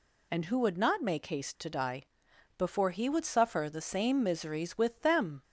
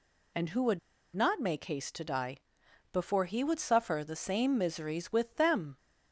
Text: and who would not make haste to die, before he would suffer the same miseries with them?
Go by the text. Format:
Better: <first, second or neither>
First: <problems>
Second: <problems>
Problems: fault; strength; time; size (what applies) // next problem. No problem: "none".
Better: first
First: none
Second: pauses between "would" and "not"; slight; at 0.7 s; 0.35 s long